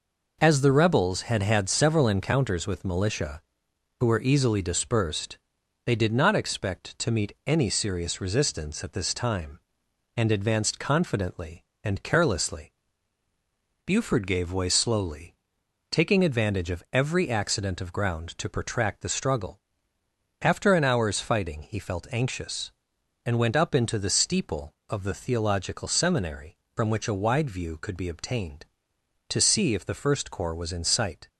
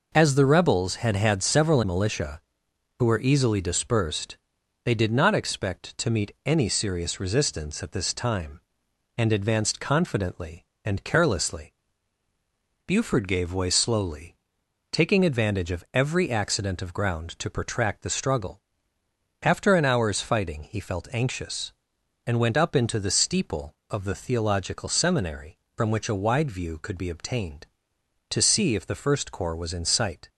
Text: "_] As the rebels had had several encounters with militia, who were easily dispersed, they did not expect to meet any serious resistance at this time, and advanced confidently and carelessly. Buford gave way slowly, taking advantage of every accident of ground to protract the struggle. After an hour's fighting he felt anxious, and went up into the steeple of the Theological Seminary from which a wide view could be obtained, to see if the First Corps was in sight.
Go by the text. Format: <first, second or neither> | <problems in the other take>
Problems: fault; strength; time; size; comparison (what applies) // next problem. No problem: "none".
first | skips "encounters with"; at 1.8 s